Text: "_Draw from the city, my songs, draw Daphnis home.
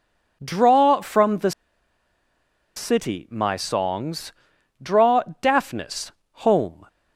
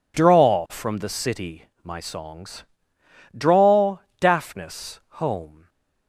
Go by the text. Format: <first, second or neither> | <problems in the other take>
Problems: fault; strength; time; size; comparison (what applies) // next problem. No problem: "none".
second | pauses between "the" and "city"; strong; at 1.5 s; 1.2 s long // pauses between "draw" and "Daphnis"; slight; at 5.2 s; 0.20 s long; slight in the second // pauses between "Daphnis" and "home"; slight; at 6.1 s; 0.30 s long; slight in the second